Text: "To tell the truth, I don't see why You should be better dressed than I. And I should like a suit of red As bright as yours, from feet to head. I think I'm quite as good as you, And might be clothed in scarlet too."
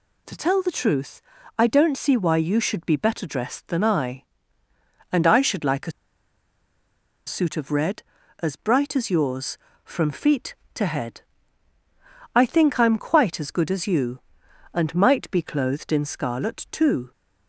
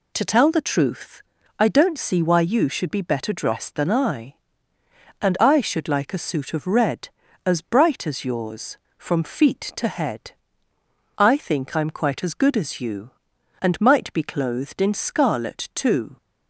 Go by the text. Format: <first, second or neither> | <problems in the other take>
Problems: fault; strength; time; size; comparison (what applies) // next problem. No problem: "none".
second | pauses between "a" and "suit"; strong; at 5.9 s; 1.3 s long